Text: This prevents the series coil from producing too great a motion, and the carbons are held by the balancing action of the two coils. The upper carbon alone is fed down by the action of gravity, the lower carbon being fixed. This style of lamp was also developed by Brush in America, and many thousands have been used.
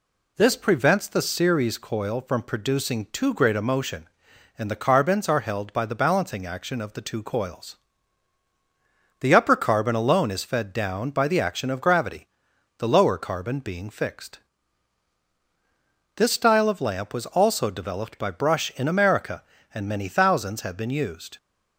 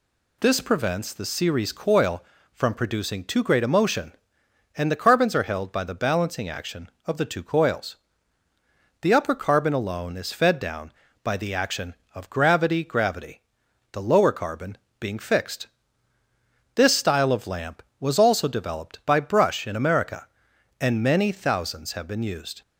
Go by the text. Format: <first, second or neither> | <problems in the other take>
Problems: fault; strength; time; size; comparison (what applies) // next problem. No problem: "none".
first | says "gravity" twice; at 12.8 s // pauses between "carbon" and "being"; slight; at 14.7 s; 0.22 s long